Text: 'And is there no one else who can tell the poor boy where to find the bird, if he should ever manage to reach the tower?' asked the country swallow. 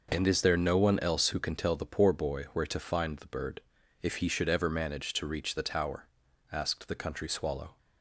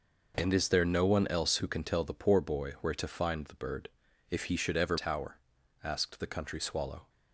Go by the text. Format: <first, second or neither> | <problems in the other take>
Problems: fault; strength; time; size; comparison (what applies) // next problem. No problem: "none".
first | skips "manage to reach the"; at 4.9 s